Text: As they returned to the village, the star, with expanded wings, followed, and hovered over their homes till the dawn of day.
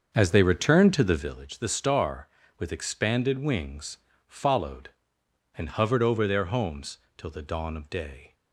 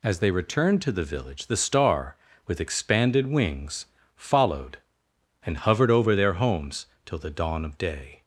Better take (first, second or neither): second